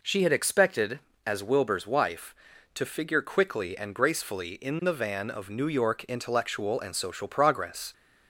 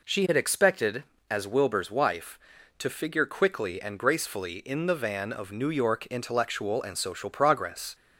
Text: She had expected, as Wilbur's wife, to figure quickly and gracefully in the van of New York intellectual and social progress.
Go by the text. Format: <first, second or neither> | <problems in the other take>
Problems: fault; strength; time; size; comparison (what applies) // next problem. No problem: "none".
neither | none